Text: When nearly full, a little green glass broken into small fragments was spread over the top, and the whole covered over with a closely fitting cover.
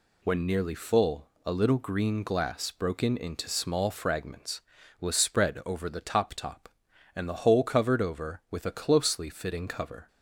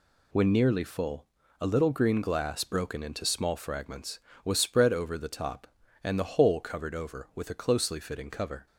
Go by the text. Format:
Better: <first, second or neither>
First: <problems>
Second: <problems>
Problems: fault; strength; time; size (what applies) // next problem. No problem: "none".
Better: second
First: says "top" twice; at 6.3 s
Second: none